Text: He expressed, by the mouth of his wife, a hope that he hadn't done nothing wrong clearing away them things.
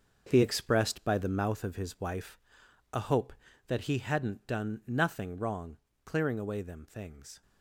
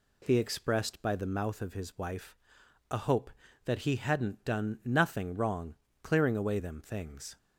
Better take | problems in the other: second | gets quieter; strong; throughout; 9.5 dB // pauses between "wrong" and "clearing"; slight; at 5.7 s; 0.26 s long; slight in the second

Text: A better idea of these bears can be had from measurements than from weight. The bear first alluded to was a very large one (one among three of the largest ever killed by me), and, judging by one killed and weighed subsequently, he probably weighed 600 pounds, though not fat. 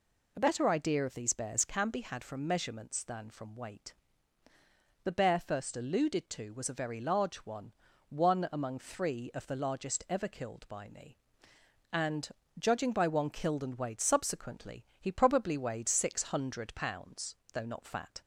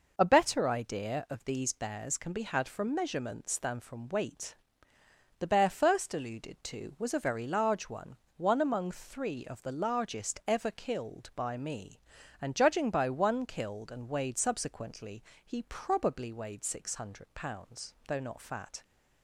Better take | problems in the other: neither | none

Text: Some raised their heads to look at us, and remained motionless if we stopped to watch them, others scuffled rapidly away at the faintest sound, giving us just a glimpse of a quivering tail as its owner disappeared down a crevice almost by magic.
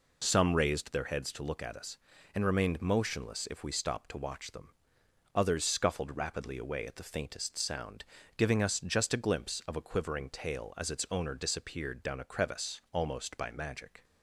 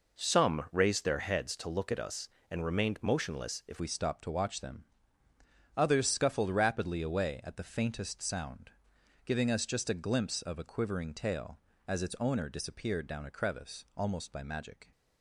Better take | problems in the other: first | changes voice at "we"; from 3.7 s on; 11.2 s long

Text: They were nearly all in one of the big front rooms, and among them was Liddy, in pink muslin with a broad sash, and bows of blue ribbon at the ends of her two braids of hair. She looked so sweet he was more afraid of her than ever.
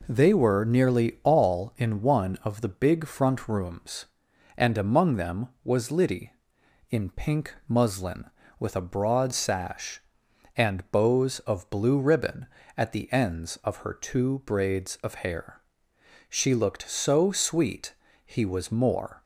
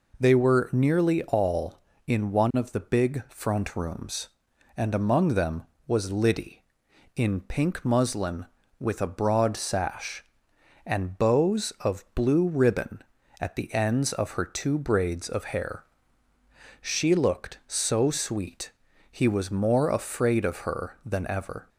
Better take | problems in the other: second | pauses between "sweet" and "he"; slight; at 17.9 s; 0.32 s long; also in the second // stops before "afraid of her than ever"; at 19.2 s

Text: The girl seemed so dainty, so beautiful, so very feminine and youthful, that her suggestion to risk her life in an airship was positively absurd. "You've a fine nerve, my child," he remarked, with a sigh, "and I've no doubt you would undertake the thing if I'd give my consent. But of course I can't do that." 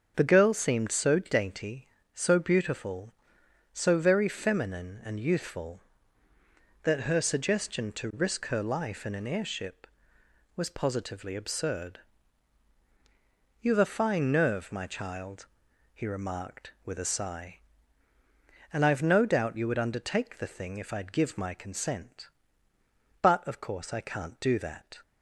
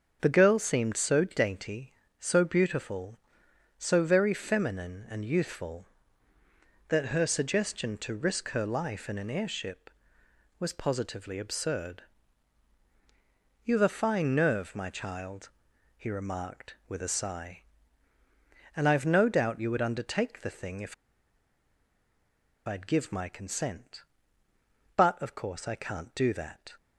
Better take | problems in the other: first | starts louder than the rest; until 1.2 s; 7 dB; also in the first // pauses between "if" and "I'd"; strong; at 20.9 s; 1.7 s long

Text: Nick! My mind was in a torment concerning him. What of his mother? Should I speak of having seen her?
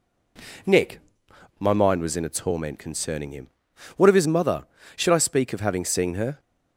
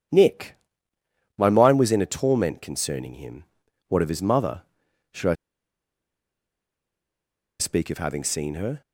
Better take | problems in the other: first | pauses between "I" and "speak"; strong; at 5.3 s; 2.2 s long

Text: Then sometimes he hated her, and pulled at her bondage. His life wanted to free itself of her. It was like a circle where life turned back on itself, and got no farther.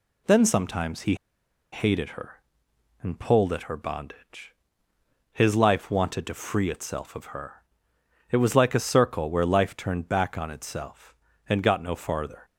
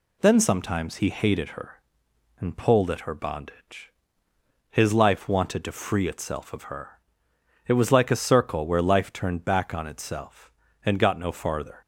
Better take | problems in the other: second | pauses between "he" and "hated"; noticeable; at 1.1 s; 0.56 s long

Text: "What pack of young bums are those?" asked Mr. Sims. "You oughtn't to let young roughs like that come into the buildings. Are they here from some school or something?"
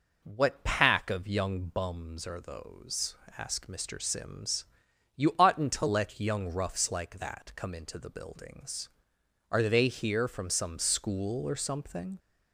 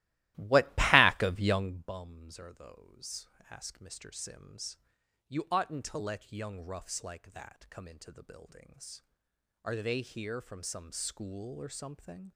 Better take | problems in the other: first | starts louder than the rest; strong; until 1.8 s; 16.5 dB

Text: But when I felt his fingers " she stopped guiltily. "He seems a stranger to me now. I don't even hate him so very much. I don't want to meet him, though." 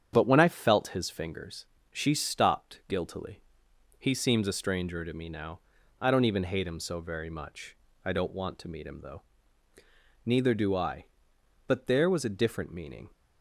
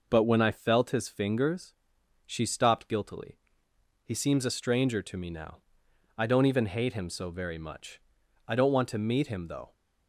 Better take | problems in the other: second | starts louder than the rest; strong; until 1.1 s; 8.5 dB // goes on to say "Neither do I But there was a different meaning"; strong; from 10.2 s on; 2.8 s long

